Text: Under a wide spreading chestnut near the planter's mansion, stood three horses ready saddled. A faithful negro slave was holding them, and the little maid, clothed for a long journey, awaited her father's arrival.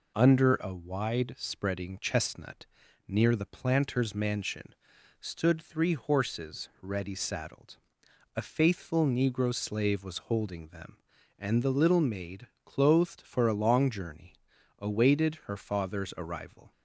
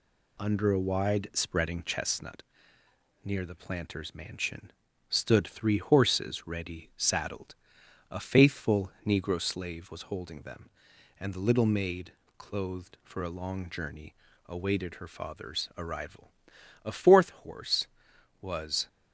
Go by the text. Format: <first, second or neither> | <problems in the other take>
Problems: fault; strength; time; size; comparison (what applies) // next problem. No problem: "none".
first | pauses between "chestnut" and "near"; noticeable; at 2.4 s; 0.80 s long; also in the first // goes on to say "A fourth horse was"; strong; from 16.7 s on; 2.0 s long